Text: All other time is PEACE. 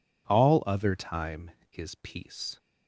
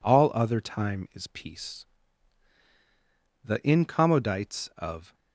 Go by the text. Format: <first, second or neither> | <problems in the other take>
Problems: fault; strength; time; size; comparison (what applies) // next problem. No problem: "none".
first | goes on to say "The Incommodites Of"; strong; from 3.4 s on; 1.7 s long